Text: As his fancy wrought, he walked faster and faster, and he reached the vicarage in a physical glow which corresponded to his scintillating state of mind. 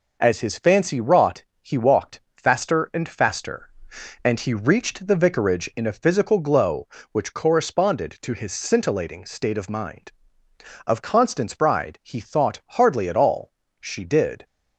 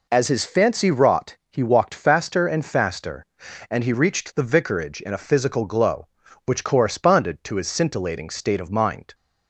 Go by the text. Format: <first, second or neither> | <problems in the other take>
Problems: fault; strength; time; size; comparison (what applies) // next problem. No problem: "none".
second | pauses between "walked" and "faster"; slight; at 2.1 s; 0.16 s long // goes on to say "Of Constance Bride he thought hardly at all She did"; strong; from 10.8 s on; 3.5 s long